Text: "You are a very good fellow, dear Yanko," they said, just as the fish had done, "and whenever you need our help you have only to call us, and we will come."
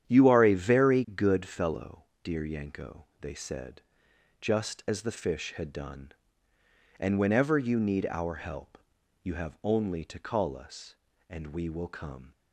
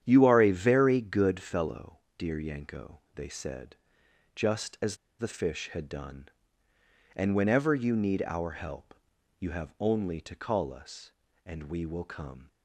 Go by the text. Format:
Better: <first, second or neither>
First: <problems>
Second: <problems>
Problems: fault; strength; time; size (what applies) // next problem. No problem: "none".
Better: first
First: starts louder than the rest; strong; until 1.1 s; 9.5 dB // pauses between "help" and "you"; at 8.7 s; 0.44 s long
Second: starts louder than the rest; strong; until 1.0 s; 9.5 dB // pauses between "as" and "the"; slight; at 4.9 s; 0.23 s long // pauses between "help" and "you"; at 8.9 s; 0.44 s long